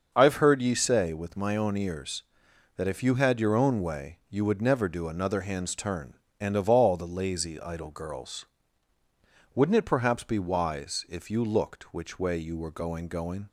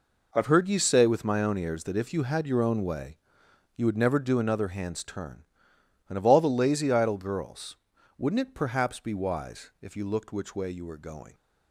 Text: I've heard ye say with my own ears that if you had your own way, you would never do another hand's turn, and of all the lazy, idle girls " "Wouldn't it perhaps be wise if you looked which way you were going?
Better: second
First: starts louder than the rest; strong; until 1.1 s; 7.5 dB // says "going" twice; at 13.0 s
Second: none

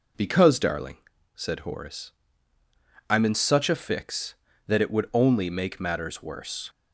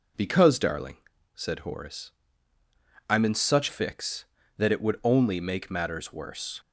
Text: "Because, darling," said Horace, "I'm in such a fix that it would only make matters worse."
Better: first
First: none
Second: skips "a"; at 3.6 s

